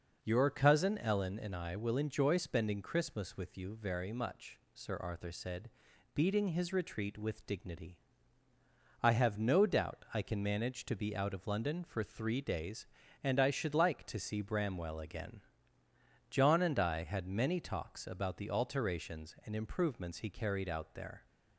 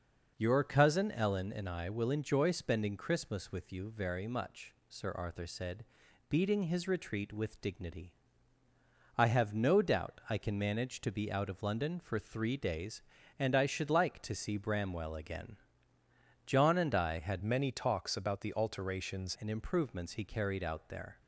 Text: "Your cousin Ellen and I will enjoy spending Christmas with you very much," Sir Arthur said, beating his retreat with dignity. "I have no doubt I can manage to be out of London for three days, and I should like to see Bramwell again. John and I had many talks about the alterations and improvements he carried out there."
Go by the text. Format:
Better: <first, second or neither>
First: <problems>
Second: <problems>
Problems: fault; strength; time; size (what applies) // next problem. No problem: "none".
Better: first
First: none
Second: changes voice from "many" to "alterations"; from 17.4 to 19.3 s; 1.9 s long